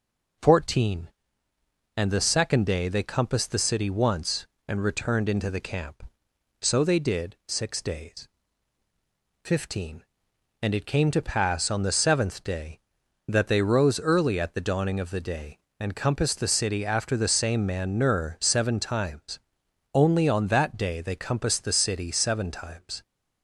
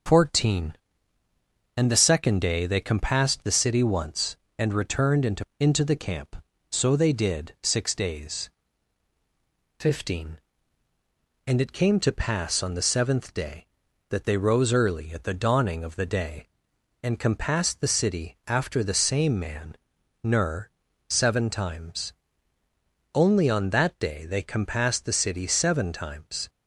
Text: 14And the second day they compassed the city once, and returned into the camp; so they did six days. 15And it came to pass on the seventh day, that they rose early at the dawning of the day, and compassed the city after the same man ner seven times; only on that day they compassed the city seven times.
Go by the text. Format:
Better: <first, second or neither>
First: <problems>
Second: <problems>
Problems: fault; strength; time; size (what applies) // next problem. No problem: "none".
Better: first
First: none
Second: starts louder than the rest; until 2.0 s; 6.5 dB // says "into" twice; at 5.5 s // pauses between "man" and "ner"; noticeable; at 19.7 s; 0.48 s long // pauses between "ner" and "seven"; at 20.6 s; 0.40 s long